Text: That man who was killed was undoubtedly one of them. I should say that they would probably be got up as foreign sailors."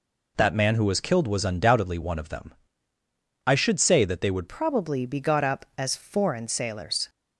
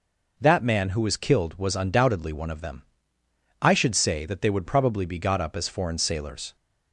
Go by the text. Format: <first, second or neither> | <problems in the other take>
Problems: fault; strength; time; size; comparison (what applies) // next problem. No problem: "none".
second | changes voice at "probably"; from 4.4 s on; 2.6 s long